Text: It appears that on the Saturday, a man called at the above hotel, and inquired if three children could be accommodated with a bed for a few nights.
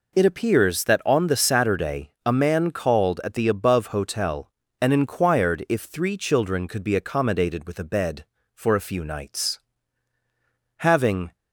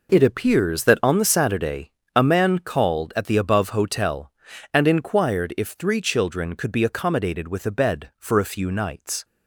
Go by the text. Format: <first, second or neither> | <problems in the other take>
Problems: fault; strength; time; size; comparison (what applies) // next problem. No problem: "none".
second | goes on to say "Having"; from 10.7 s on; 0.56 s long